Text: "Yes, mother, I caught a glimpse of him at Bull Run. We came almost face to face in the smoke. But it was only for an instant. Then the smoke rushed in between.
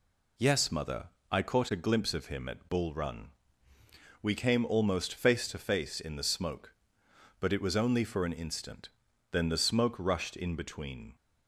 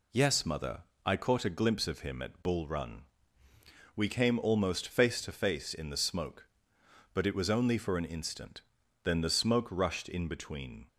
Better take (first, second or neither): neither